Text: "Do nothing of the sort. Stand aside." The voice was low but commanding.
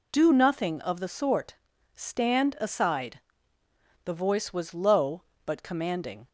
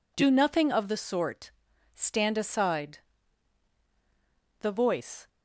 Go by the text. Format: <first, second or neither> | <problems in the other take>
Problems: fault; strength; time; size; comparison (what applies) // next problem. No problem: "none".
first | stops before "was low but commanding"; at 5.2 s